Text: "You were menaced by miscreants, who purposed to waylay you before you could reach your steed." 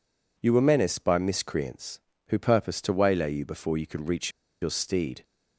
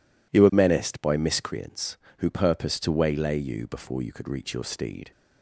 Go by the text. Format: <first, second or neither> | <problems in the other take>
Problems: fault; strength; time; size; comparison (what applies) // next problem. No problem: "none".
second | pauses between "reach" and "your"; slight; at 4.2 s; 0.32 s long